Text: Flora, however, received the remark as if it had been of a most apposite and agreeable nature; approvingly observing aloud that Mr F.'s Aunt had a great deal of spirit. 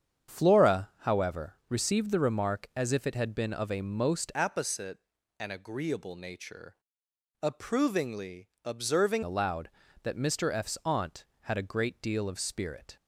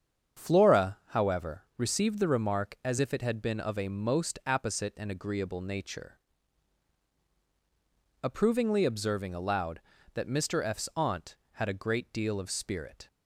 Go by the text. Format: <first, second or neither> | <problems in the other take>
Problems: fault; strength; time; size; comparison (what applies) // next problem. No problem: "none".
second | starts louder than the rest; strong; until 1.4 s; 8 dB; strong in the second // changes voice from "apposite" to "observing"; from 4.3 to 9.2 s; 4.9 s long // pauses between "approvingly" and "observing"; slight; at 8.4 s; 0.16 s long